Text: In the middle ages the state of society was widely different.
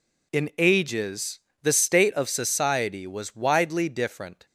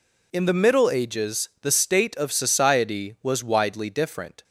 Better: second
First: skips "the middle"; at 0.5 s // pauses between "ages" and "the"; slight; at 1.3 s; 0.22 s long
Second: none

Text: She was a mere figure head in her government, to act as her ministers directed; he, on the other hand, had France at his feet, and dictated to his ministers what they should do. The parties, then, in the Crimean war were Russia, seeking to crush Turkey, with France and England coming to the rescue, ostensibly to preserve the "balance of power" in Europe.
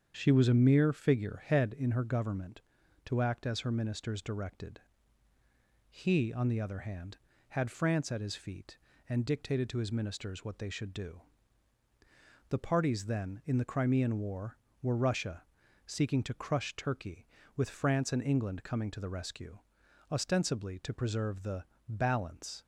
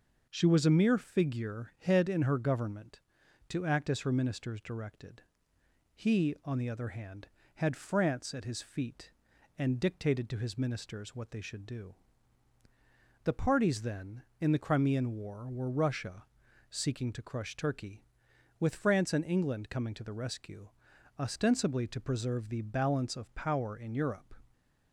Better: second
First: starts louder than the rest; strong; until 1.1 s; 7.5 dB // pauses between "the" and "balance"; slight; at 21.6 s; 0.24 s long // stops before "of power in Europe"; at 22.6 s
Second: none

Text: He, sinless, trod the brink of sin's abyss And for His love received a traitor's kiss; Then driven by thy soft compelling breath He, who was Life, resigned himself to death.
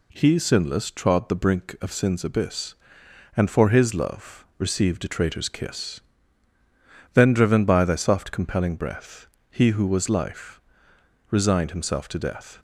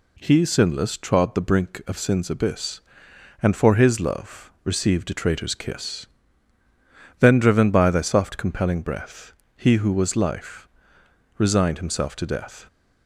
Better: neither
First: pauses between "breath" and "He"; slight; at 9.2 s; 0.22 s long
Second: pauses between "breath" and "He"; slight; at 9.3 s; 0.22 s long

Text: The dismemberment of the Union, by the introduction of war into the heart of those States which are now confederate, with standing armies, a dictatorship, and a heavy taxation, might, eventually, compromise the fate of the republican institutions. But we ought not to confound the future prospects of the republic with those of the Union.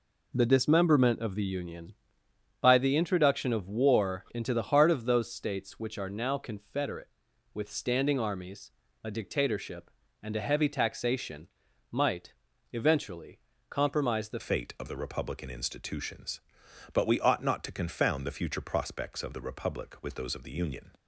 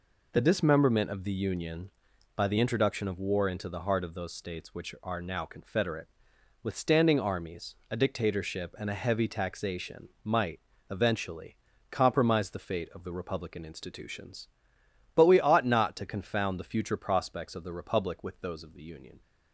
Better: second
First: changes voice at "fate"; from 14.3 s on; 6.6 s long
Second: none

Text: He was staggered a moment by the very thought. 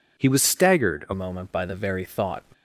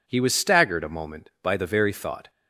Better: second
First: changes voice at "moment"; from 1.1 s on; 1.3 s long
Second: none

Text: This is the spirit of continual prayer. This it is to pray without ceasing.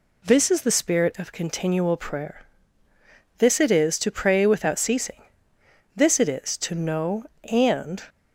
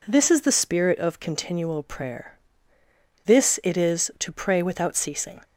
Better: second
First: goes on to say "This it is to know and"; strong; from 5.9 s on; 2.0 s long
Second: none

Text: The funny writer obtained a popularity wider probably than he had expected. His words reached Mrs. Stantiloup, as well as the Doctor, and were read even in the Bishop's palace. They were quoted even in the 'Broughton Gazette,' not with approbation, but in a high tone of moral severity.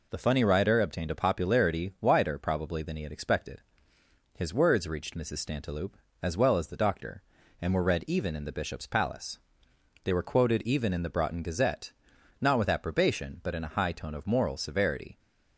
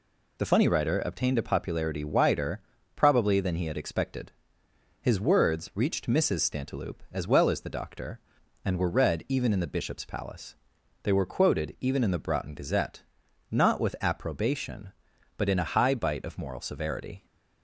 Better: first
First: none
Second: pauses between "wider" and "probably"; slight; at 2.5 s; 0.36 s long // says "bite" for "tone"; at 15.9 s

